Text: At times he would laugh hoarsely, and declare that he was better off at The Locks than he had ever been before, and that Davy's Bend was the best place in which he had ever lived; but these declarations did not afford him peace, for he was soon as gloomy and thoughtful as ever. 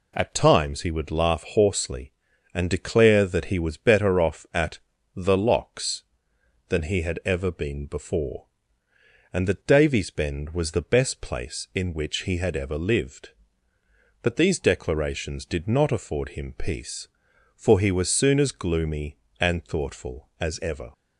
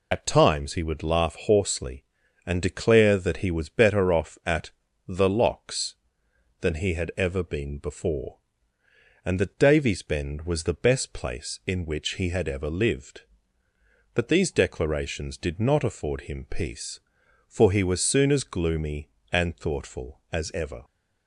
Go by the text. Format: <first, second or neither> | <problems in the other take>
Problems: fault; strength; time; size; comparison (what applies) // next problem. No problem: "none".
first | loses the start of "At"; at 0.1 s; 60 ms // pauses between "at" and "The"; at 4.7 s; 0.38 s long; also in the first